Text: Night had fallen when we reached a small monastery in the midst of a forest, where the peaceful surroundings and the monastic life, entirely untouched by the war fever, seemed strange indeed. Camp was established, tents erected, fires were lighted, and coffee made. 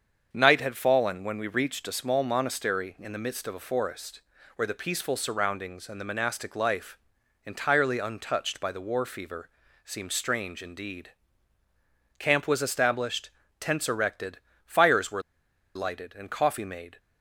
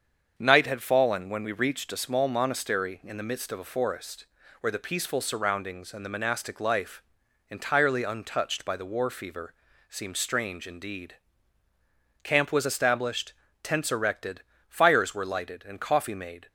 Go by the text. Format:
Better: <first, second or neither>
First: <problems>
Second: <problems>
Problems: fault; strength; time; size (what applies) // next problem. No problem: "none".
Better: second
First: starts louder than the rest; strong; until 1.3 s; 7 dB // pauses between "were" and "lighted"; noticeable; at 15.2 s; 0.54 s long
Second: starts louder than the rest; strong; until 1.3 s; 7 dB